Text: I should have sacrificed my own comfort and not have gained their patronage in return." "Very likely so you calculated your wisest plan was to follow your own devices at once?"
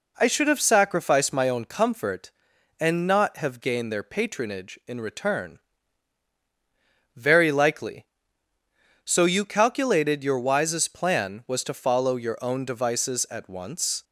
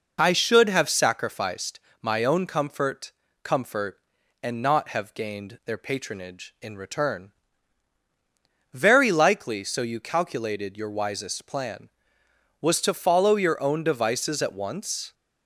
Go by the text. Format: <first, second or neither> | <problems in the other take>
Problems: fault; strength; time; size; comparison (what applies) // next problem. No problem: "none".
first | pauses between "sacrificed" and "my"; slight; at 1.7 s; 0.22 s long // says "comfort" twice; at 3.4 s